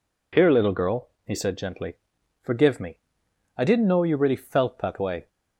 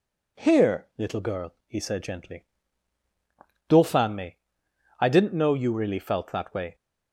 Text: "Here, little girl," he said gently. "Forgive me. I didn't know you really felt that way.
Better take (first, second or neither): first